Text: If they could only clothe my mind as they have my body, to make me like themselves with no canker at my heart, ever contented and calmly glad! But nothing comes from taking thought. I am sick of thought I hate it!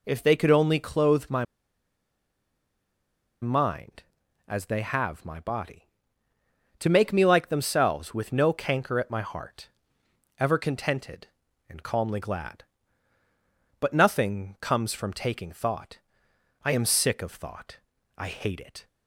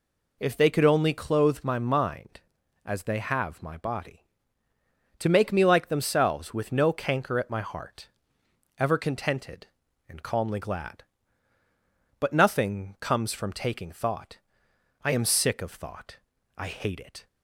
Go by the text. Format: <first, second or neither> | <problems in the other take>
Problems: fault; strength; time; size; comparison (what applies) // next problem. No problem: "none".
second | pauses between "my" and "mind"; strong; at 1.4 s; 1.9 s long // pauses between "thought" and "I"; at 17.7 s; 0.40 s long; also in the second